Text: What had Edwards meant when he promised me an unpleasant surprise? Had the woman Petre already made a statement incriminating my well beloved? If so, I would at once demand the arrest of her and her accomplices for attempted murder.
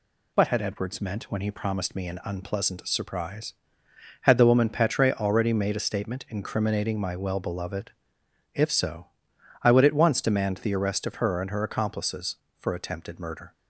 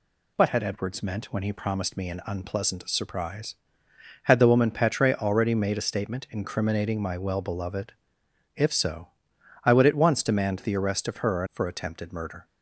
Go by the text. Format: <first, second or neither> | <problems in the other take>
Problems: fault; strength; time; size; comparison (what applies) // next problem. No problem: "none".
first | skips "and her accomplices"; at 11.4 s